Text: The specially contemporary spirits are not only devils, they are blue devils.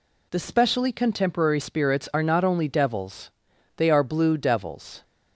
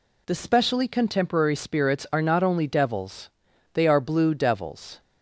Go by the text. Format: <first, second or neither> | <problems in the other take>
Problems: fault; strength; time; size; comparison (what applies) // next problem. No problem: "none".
neither | none